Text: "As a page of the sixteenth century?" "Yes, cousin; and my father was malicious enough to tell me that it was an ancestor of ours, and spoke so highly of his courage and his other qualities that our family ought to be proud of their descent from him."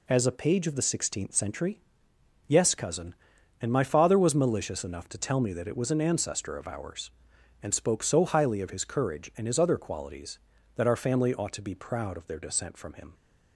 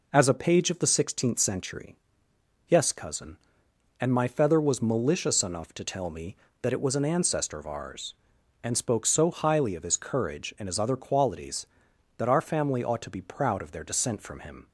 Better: first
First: none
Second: says "feather" for "father"; at 4.2 s

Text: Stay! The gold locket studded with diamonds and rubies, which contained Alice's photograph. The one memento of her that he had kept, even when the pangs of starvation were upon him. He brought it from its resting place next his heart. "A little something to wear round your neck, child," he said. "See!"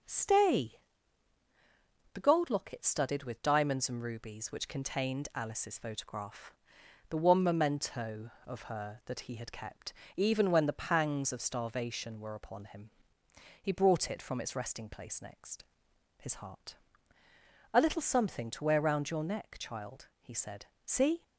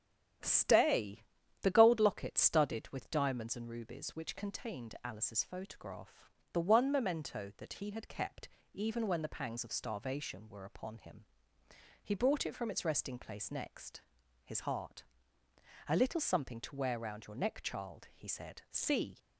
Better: first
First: starts louder than the rest; until 2.3 s; 7 dB // pauses between "next" and "his"; noticeable; at 15.6 s; 0.56 s long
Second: starts louder than the rest; strong; until 1.8 s; 9 dB // skips "of her"; at 7.5 s // pauses between "next" and "his"; noticeable; at 13.9 s; 0.46 s long

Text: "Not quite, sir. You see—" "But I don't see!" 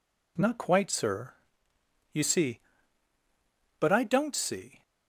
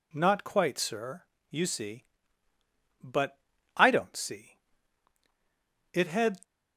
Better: first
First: none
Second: pauses between "But" and "I"; at 3.3 s; 0.38 s long // goes on to say "It had"; slight; from 5.9 s on; 0.48 s long

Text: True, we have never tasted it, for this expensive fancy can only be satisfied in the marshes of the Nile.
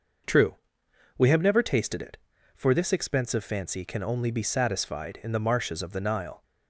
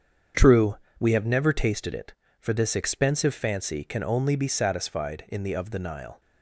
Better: first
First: none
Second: starts louder than the rest; strong; until 1.5 s; 7.5 dB // skips "marshes"; at 5.5 s

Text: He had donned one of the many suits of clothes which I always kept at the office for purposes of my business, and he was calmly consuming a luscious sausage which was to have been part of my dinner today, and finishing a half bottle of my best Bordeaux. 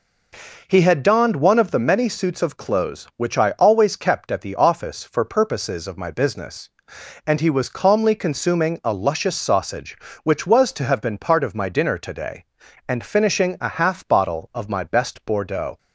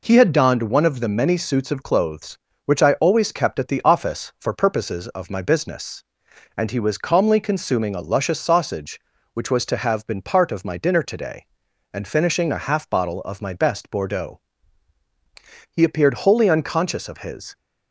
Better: first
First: none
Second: goes on to say "He appeared wholly unconscious of his"; strong; from 15.6 s on; 1.8 s long

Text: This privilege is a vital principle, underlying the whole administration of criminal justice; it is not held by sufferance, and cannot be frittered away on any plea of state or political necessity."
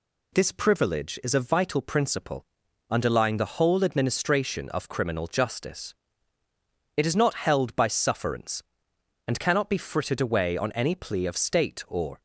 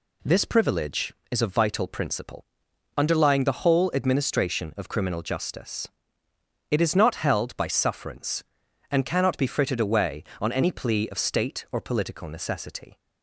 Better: second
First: stops before "political necessity"; at 12.1 s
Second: none

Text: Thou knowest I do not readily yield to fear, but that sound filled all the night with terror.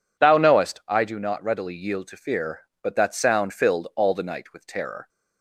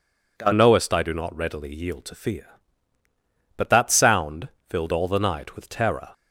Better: first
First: none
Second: changes voice at "knowest"; from 0.5 s on; 5.5 s long // pauses between "sound" and "filled"; slight; at 4.4 s; 0.22 s long

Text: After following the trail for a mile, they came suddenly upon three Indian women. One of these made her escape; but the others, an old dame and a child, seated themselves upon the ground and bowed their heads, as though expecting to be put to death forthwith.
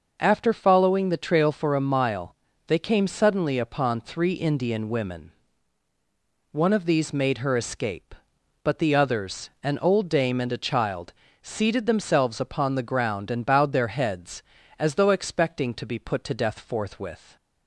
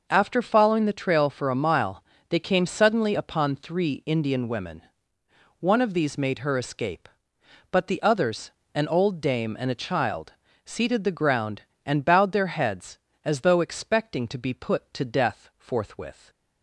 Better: first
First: none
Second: skips "themselves upon"; at 11.0 s

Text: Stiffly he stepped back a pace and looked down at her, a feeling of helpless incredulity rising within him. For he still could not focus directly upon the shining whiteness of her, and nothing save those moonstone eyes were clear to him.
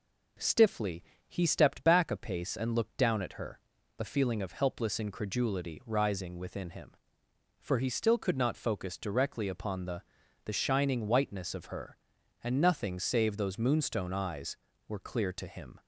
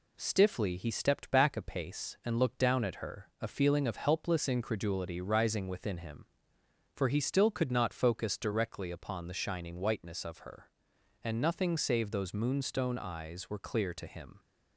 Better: second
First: pauses between "Stiffly" and "he"; slight; at 1.0 s; 0.26 s long // says "the" twice; at 10.4 s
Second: none

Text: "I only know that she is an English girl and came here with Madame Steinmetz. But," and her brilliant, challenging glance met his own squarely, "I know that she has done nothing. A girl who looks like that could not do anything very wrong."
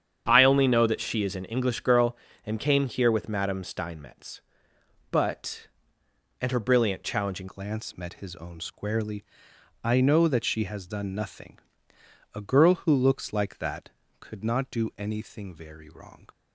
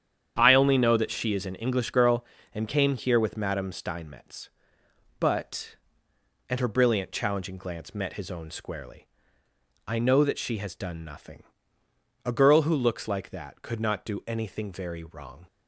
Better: second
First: starts louder than the rest; strong; until 1.2 s; 8.5 dB // changes voice at "glance"; from 7.4 s on; 8.8 s long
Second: starts louder than the rest; strong; until 1.3 s; 9 dB

